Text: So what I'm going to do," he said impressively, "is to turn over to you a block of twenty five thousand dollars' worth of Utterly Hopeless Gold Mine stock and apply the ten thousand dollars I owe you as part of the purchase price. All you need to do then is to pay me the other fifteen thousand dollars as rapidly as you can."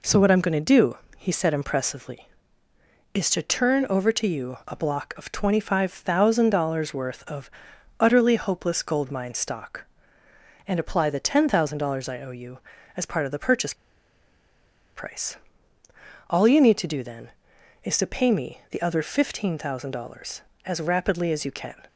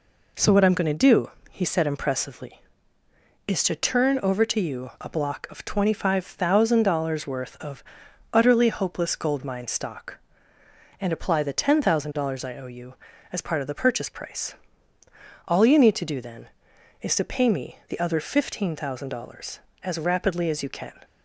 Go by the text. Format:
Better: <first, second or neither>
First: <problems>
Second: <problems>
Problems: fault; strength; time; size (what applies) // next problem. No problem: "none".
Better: second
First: pauses between "of" and "Utterly"; noticeable; at 7.5 s; 0.48 s long // pauses between "purchase" and "price"; at 13.7 s; 1.2 s long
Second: pauses between "of" and "Utterly"; noticeable; at 7.8 s; 0.48 s long